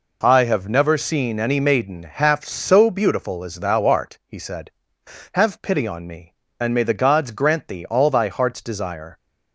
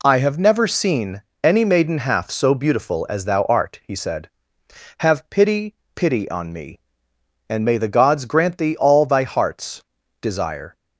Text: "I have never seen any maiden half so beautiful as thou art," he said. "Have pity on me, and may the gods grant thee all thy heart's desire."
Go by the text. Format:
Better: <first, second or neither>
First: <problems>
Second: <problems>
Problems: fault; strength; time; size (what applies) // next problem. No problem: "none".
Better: first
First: none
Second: pauses between "seen" and "any"; slight; at 1.2 s; 0.22 s long // says "pity" twice; at 5.9 s // pauses between "heart's" and "desire"; slight; at 9.8 s; 0.36 s long